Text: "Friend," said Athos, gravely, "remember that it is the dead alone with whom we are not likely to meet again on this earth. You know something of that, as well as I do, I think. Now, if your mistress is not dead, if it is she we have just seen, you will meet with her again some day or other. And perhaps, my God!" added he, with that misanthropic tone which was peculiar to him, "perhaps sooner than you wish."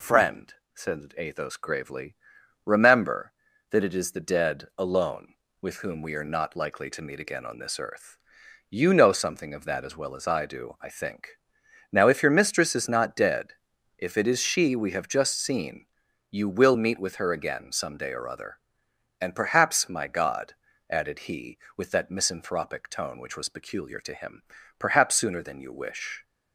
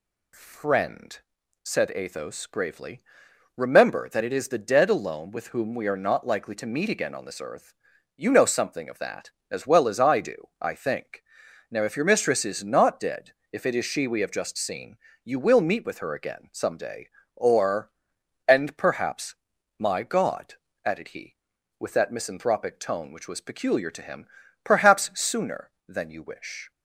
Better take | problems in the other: first | skips "other"; at 18.1 s

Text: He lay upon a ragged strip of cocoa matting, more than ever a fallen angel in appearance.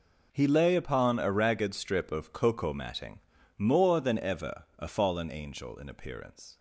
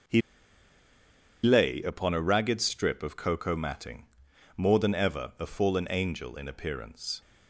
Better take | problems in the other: first | starts louder than the rest; noticeable; until 2.3 s; 6 dB // pauses between "He" and "lay"; at 0.2 s; 1.2 s long

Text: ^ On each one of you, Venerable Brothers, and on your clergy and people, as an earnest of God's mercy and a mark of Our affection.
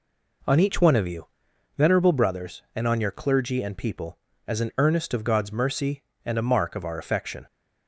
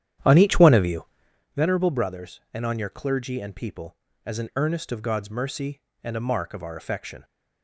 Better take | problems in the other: first | starts louder than the rest; strong; until 1.5 s; 10.5 dB

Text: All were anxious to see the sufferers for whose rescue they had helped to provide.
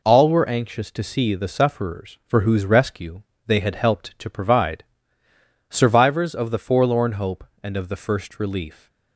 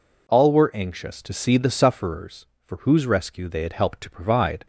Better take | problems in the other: second | pauses between "rescue" and "they"; slight; at 3.2 s; 0.24 s long // goes on to say "Survivors of the Forlorn Hope and of the First Relief"; strong; from 5.6 s on; 3.1 s long

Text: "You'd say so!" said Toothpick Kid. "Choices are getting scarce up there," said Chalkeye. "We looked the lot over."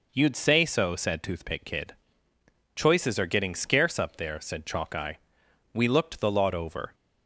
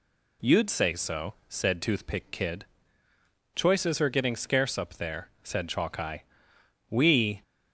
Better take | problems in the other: first | stops before "looked the lot over"; at 7.4 s

